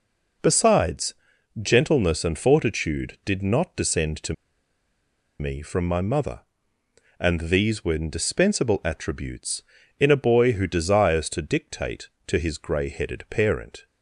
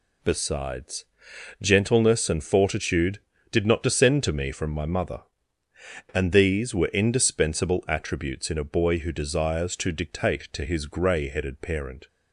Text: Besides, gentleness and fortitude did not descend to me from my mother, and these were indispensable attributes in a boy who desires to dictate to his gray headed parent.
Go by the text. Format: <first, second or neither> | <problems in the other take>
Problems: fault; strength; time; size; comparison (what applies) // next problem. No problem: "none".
second | pauses between "to" and "me"; at 4.3 s; 1.0 s long